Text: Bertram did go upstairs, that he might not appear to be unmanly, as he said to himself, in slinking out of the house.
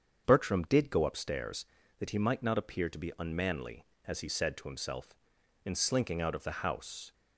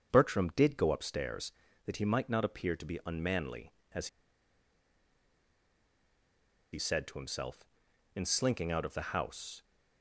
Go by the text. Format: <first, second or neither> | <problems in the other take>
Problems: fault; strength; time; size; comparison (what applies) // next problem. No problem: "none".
first | starts louder than the rest; strong; until 1.1 s; 7.5 dB; strong in the first // pauses between "as" and "he"; strong; at 4.0 s; 2.6 s long